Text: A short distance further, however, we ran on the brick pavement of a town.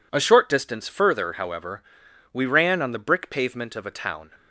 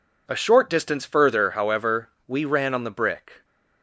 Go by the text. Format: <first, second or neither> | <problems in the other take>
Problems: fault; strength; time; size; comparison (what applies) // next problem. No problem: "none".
first | stops before "pavement of a town"; at 3.4 s